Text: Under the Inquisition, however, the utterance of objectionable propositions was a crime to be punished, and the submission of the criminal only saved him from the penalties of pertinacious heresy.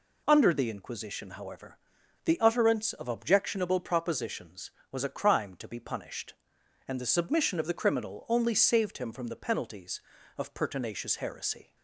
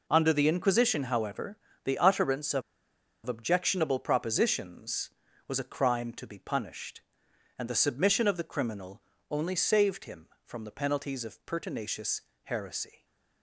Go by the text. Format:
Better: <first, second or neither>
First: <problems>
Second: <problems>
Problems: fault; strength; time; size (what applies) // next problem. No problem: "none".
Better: first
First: none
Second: pauses between "of" and "objectionable"; noticeable; at 2.6 s; 0.64 s long // pauses between "criminal" and "only"; slight; at 9.0 s; 0.30 s long // pauses between "pertinacious" and "heresy"; slight; at 12.2 s; 0.24 s long